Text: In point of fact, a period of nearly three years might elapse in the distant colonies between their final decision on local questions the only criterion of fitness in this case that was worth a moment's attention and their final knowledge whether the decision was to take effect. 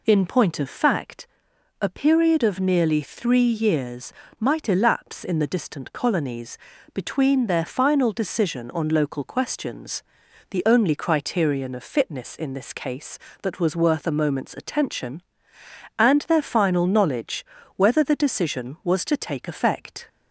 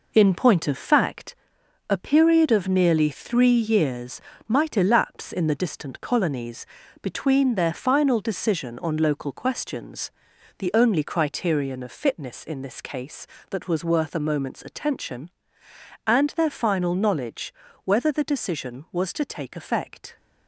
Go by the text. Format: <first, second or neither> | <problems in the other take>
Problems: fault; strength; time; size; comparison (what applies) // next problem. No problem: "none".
first | gets quieter; throughout; 6.5 dB // pauses between "years" and "might"; slight; at 4.1 s; 0.26 s long; slight in the first // pauses between "colonies" and "between"; slight; at 6.6 s; 0.34 s long; slight in the first // pauses between "questions" and "the"; noticeable; at 10.0 s; 0.48 s long; noticeable in the first // pauses between "knowledge" and "whether"; slight; at 17.5 s; 0.30 s long; slight in the first